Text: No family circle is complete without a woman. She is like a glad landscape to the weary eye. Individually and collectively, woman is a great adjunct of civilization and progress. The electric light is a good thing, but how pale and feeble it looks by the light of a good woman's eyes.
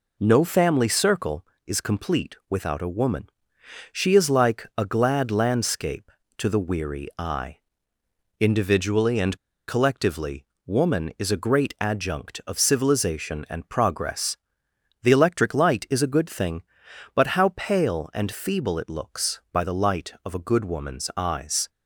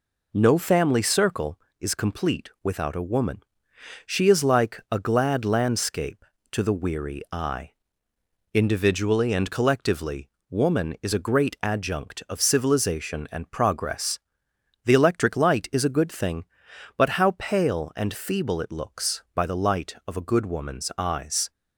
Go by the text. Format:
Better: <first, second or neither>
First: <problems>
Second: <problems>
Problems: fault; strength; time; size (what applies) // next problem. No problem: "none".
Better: second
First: pauses between "and" and "collectively"; slight; at 9.3 s; 0.32 s long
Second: none